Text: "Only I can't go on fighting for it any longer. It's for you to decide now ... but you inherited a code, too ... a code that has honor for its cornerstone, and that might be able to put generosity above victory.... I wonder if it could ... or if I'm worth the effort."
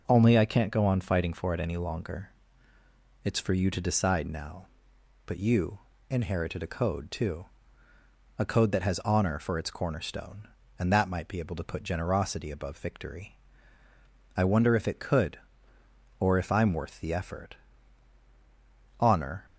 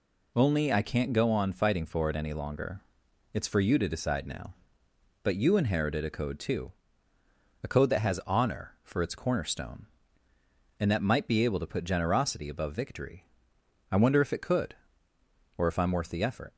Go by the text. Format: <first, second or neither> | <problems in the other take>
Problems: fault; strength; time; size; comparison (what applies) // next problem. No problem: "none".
second | pauses between "you" and "inherited"; slight; at 5.7 s; 0.32 s long // goes on to say "Honor"; slight; from 18.9 s on; 0.46 s long